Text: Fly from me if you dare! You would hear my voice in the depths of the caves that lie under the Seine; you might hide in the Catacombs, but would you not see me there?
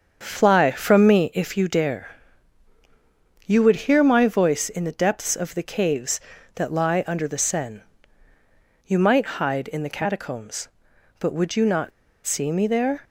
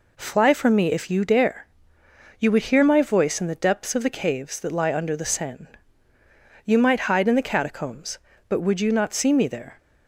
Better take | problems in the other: second | starts louder than the rest; until 1.2 s; 7 dB // pauses between "not" and "see"; slight; at 11.9 s; 0.33 s long

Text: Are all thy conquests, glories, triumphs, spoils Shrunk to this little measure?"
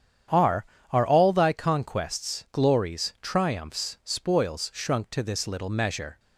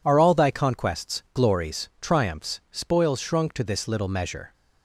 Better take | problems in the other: second | starts louder than the rest; strong; until 1.6 s; 9 dB // says "Are" twice; at 0.9 s

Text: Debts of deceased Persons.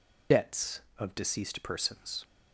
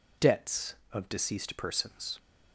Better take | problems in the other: second | loses the start of "Debts"; at 0.3 s; 50 ms

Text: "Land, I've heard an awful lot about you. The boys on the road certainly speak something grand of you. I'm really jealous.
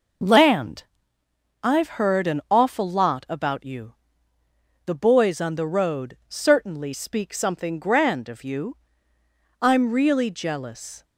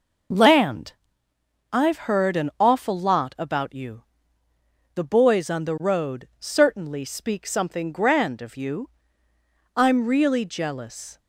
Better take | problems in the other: neither | none

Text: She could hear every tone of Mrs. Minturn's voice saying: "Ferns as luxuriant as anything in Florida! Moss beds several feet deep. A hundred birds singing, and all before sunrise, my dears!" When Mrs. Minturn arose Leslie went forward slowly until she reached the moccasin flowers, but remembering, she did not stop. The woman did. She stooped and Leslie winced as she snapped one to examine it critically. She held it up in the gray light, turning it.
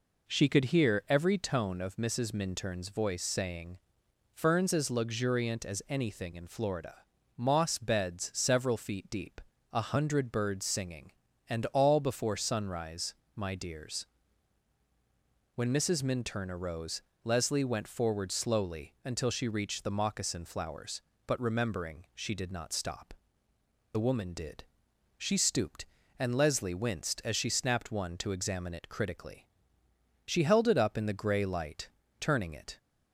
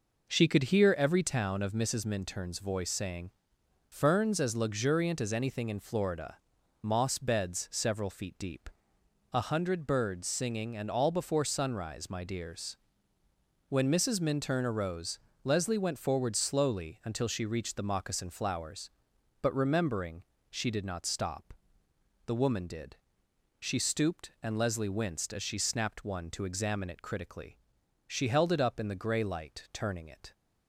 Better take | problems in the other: first | says "town" for "tone"; at 1.2 s // pauses between "arose" and "Leslie"; slight; at 15.1 s; 0.24 s long; slight in the first

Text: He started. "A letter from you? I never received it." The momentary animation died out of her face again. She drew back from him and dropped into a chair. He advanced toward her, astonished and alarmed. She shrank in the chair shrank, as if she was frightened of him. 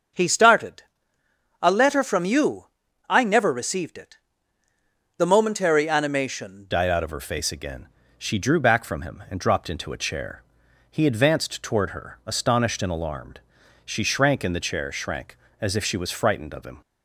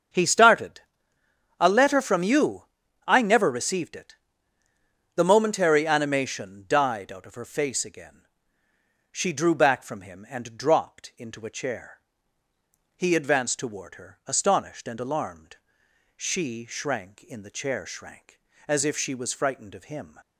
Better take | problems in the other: second | starts louder than the rest; strong; until 1.9 s; 7 dB; strong in the second // changes voice at "died"; from 6.7 s on; 10.0 s long

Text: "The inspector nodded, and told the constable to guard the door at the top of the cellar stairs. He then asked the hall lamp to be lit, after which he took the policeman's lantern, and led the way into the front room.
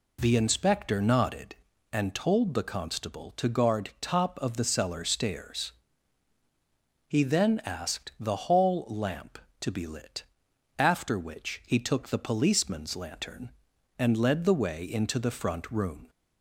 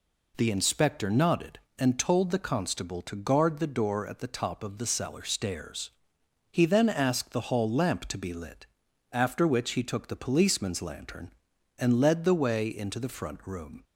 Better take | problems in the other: second | skips "the door at the"; at 3.9 s

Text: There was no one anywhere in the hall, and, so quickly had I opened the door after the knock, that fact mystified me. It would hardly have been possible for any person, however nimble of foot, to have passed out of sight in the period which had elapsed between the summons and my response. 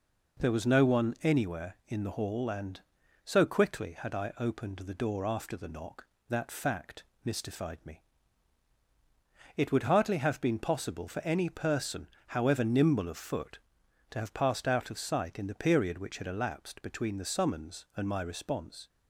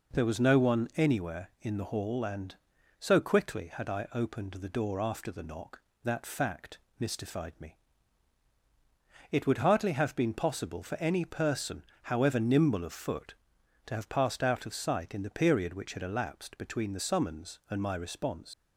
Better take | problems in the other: first | pauses between "fact" and "mystified"; slight; at 6.7 s; 0.22 s long; slight in the first // leaves "response" unfinished; at 18.5 s; 80 ms

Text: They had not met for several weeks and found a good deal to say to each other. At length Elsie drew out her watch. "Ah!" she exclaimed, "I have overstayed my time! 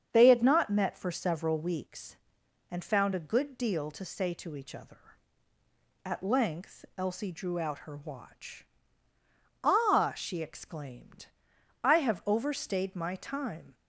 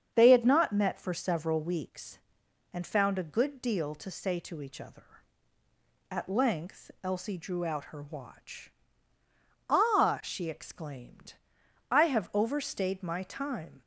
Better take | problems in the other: neither | starts louder than the rest; strong; the same in both

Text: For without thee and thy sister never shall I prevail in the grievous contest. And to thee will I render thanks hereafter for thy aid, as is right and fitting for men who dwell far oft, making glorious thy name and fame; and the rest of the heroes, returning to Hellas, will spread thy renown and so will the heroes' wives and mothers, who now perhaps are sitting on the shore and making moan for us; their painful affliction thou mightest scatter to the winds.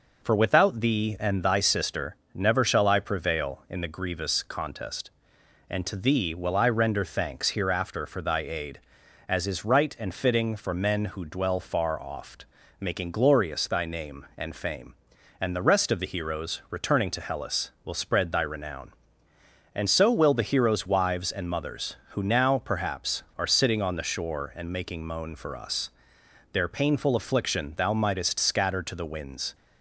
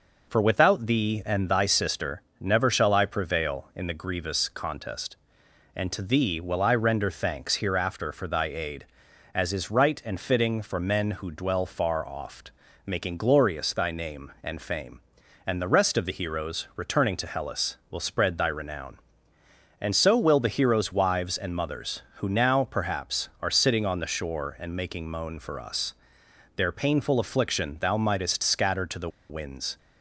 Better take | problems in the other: first | pauses between "sister" and "never"; slight; at 2.2 s; 0.18 s long; slight in the first // pauses between "the" and "winds"; slight; at 29.0 s; 0.21 s long

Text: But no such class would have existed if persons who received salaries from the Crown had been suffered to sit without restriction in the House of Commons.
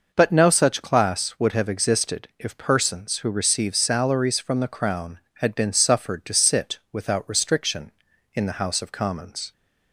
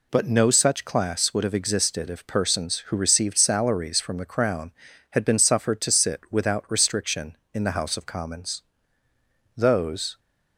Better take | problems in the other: first | goes on to say "Those"; noticeable; from 9.5 s on; 0.64 s long

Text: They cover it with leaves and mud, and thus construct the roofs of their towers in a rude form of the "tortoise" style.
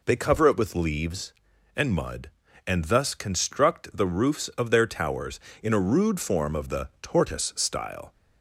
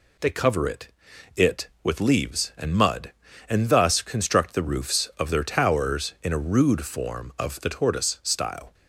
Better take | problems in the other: first | says "it" twice; at 1.3 s

